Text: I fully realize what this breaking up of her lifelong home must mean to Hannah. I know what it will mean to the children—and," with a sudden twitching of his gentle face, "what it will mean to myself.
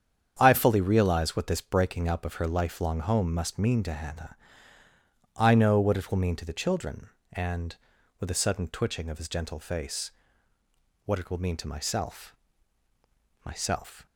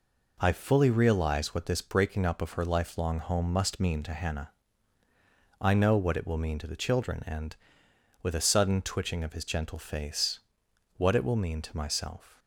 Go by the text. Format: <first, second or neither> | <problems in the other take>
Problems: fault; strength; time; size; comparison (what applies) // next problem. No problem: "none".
second | starts louder than the rest; strong; until 1.4 s; 8 dB // says "myself" twice; at 13.4 s